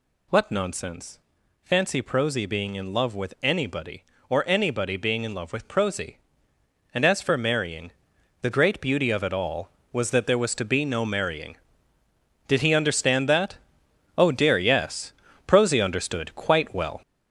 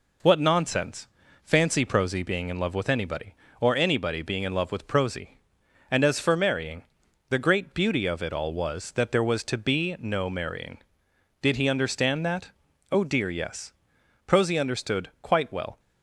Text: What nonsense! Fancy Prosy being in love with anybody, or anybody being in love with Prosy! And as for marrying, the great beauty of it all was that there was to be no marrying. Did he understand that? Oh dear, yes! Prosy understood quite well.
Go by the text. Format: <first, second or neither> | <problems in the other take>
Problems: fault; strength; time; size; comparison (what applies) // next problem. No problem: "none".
second | gets louder; noticeable; throughout; 5.5 dB